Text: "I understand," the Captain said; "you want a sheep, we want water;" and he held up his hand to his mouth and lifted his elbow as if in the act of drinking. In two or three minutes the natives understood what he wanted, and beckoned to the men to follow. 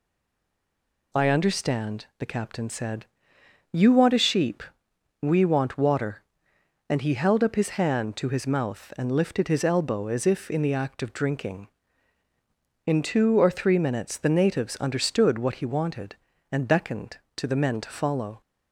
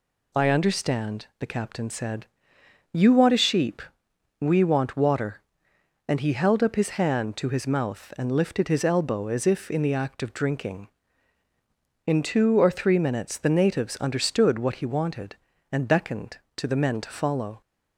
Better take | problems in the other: second | stays silent before the first word; until 1.1 s; 1.1 s long

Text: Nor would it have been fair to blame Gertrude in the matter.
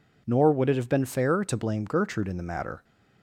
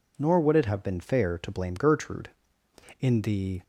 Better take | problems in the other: first | stops before "matter"; at 3.6 s

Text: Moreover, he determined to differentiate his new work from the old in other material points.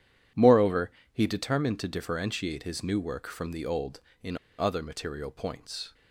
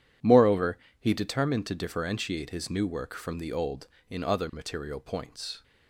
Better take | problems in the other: second | pauses between "in" and "other"; slight; at 4.3 s; 0.21 s long

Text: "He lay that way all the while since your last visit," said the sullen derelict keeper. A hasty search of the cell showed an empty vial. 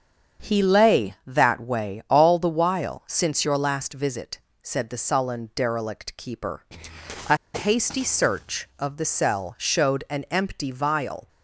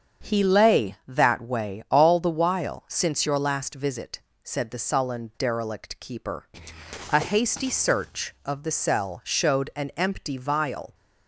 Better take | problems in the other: second | starts louder than the rest; until 1.5 s; 7 dB; also in the second // pauses between "A" and "hasty"; slight; at 7.3 s; 0.17 s long

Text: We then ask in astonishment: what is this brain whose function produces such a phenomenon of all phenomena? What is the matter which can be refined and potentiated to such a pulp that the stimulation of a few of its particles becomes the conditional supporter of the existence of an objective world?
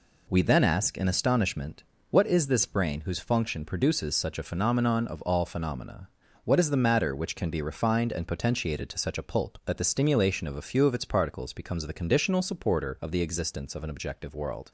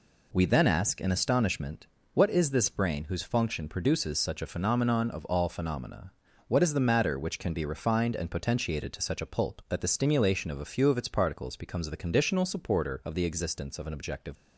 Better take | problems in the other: first | stops before "world"; at 14.3 s

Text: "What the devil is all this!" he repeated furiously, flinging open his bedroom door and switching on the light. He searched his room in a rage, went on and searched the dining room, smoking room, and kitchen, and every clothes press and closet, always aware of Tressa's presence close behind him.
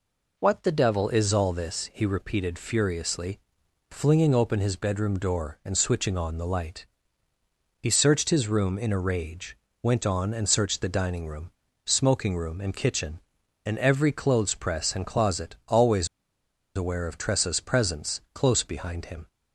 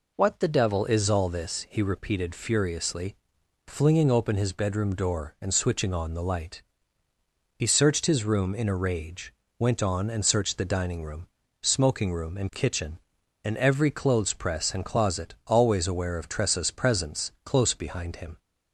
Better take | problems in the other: second | pauses between "always" and "aware"; noticeable; at 16.0 s; 0.68 s long

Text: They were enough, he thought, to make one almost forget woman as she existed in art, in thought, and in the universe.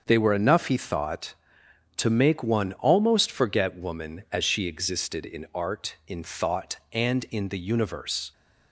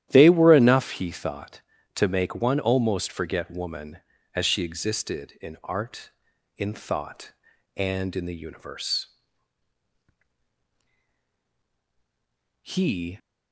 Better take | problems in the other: first | starts louder than the rest; strong; until 1.1 s; 12 dB; also in the first // goes on to say "He"; from 12.6 s on; 0.56 s long

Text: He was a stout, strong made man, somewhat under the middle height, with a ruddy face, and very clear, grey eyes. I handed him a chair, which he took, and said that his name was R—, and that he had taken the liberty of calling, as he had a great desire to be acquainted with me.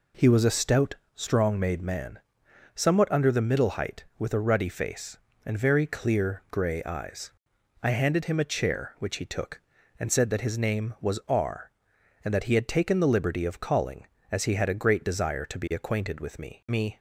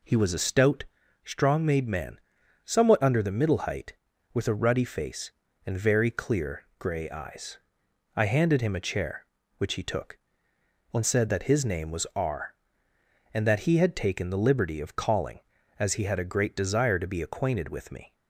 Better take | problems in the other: second | says "me" twice; at 16.6 s

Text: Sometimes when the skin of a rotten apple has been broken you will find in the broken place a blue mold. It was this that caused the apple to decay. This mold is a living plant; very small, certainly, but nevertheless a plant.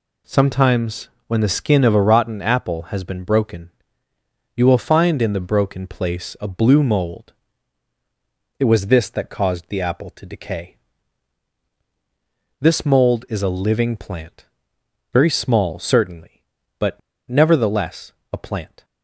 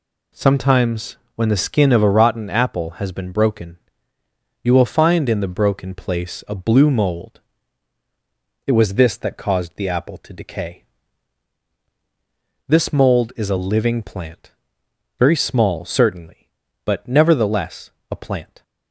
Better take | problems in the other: second | pauses between "Sometimes" and "when"; slight; at 1.0 s; 0.18 s long; slight in the second // pauses between "broken" and "you"; noticeable; at 3.6 s; 0.88 s long; noticeable in the second // pauses between "but" and "nevertheless"; slight; at 17.0 s; 0.30 s long // pauses between "nevertheless" and "a"; slight; at 18.1 s; 0.18 s long; slight in the second

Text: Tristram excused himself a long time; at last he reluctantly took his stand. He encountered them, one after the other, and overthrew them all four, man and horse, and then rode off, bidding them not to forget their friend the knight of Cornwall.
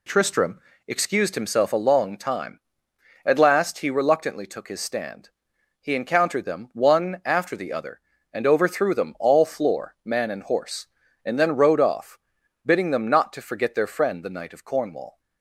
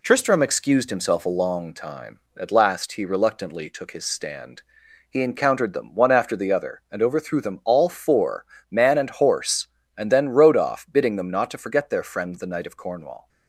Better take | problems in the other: second | pauses between "Tristram" and "excused"; slight; at 0.5 s; 0.28 s long // says "floor" for "four"; at 9.4 s

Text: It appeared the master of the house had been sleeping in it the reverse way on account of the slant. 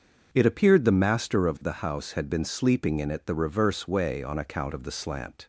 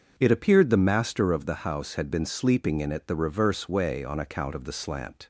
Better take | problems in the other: neither | starts louder than the rest; the same in both

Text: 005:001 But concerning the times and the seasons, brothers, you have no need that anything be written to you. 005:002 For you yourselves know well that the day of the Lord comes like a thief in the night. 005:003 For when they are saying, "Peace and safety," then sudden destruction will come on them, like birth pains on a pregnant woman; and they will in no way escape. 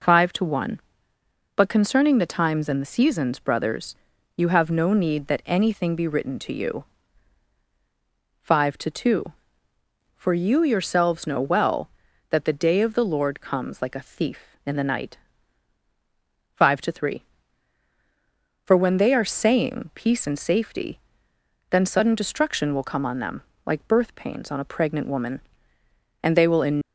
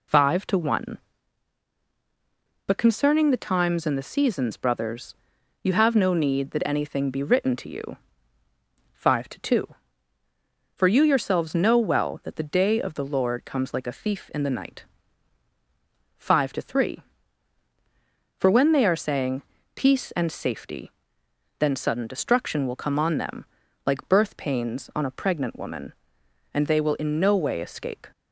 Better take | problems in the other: second | stops before "no way escape"; at 26.8 s

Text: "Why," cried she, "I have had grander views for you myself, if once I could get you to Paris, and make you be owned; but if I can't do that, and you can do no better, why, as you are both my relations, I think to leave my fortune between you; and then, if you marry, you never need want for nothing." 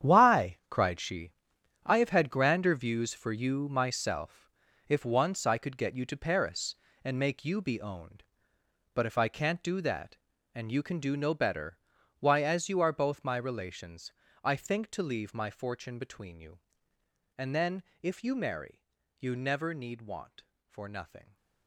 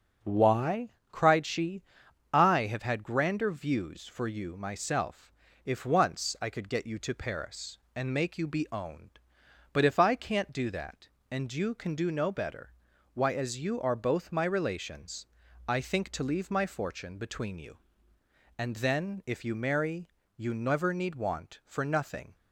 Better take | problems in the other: second | gets quieter; strong; throughout; 13 dB // starts louder than the rest; strong; until 1.1 s; 9 dB; also in the second

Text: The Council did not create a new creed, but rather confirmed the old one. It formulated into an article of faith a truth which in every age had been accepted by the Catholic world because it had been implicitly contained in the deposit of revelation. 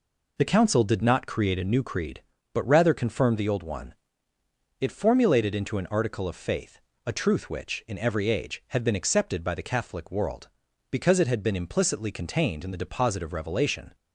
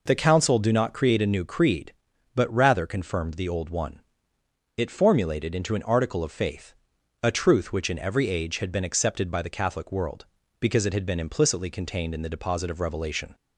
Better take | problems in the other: first | says "do" for "did"; at 0.5 s // pauses between "faith" and "a"; noticeable; at 6.7 s; 0.50 s long; slight in the first

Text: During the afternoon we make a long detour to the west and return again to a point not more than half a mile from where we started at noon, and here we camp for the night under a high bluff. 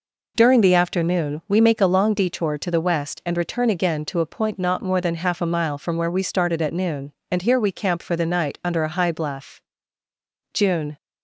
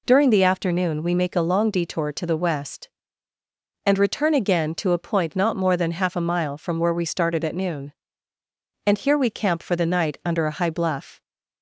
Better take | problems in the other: second | goes on to say "June"; slight; from 10.5 s on; 0.44 s long

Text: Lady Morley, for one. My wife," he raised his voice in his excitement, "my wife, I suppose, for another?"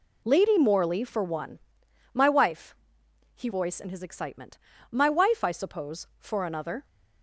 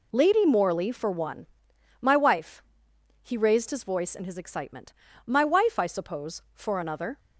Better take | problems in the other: second | skips "raised his"; at 3.4 s

